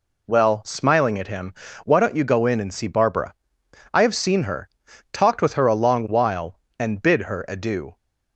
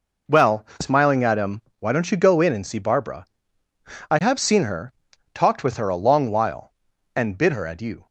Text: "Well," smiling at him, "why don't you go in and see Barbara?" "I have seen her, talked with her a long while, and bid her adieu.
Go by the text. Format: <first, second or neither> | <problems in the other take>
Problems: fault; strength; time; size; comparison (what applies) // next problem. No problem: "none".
neither | none